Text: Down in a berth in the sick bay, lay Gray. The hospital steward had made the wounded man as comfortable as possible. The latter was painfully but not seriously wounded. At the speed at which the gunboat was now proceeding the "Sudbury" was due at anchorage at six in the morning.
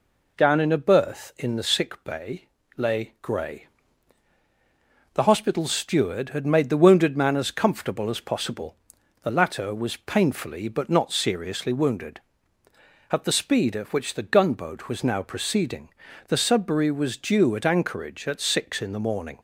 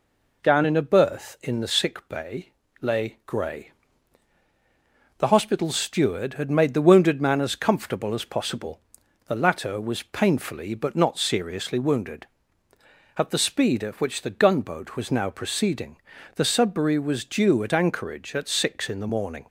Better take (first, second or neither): neither